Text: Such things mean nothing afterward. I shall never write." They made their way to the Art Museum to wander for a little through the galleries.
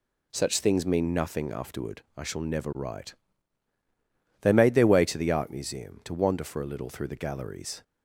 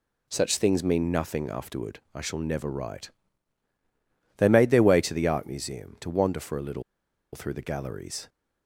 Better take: first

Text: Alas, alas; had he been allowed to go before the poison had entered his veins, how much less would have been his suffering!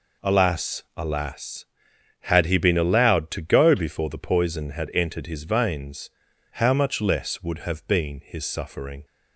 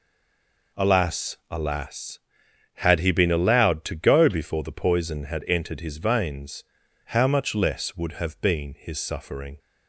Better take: first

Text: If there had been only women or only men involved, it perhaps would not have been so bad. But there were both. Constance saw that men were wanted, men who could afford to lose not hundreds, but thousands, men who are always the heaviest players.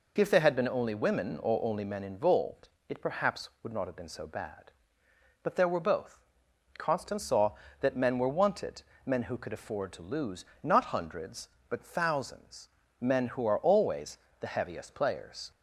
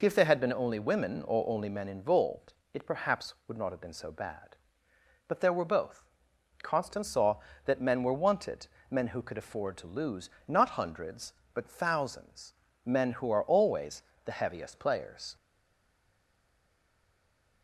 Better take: first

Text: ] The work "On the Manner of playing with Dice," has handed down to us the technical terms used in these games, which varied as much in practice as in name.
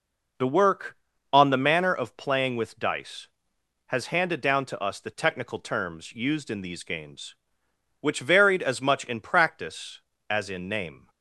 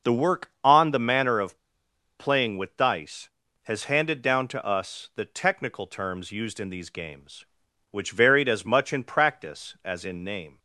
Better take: first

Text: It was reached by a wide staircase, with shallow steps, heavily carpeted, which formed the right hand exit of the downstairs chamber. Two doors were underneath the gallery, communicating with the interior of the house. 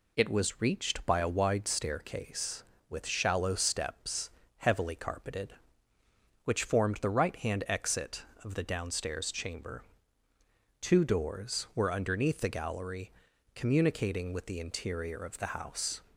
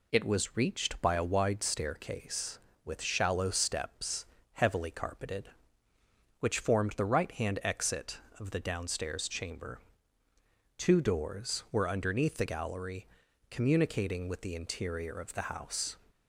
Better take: neither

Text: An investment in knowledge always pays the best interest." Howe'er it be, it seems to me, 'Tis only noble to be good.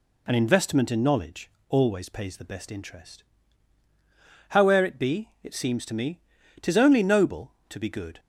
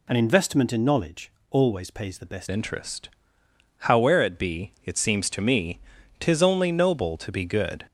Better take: first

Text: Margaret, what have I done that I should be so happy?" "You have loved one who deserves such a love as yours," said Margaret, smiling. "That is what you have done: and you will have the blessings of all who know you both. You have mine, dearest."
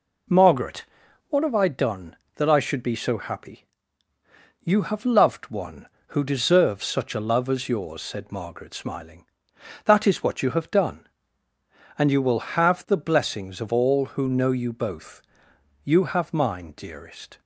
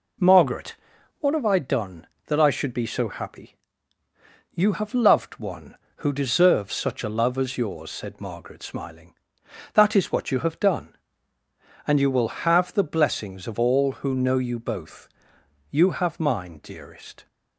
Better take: neither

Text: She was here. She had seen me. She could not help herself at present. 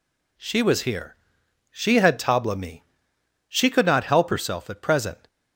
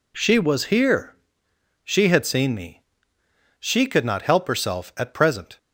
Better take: second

